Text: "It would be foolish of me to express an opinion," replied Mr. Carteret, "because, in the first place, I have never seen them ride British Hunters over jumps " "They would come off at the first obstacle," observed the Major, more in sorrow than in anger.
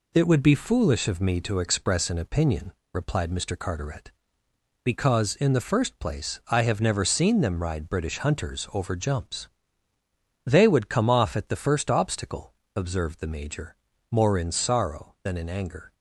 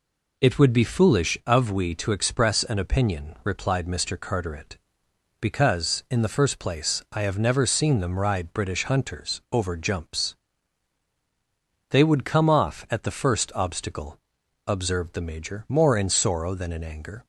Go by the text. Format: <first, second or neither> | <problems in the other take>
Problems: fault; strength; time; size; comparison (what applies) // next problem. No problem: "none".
first | says "we" for "me"; at 1.7 s